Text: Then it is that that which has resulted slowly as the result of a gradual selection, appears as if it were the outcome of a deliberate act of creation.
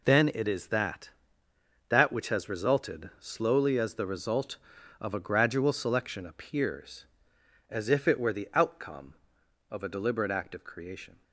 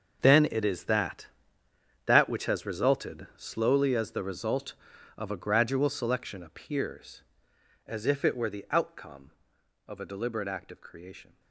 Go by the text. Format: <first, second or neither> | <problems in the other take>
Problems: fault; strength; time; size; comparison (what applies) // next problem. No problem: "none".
first | gets quieter; strong; throughout; 15 dB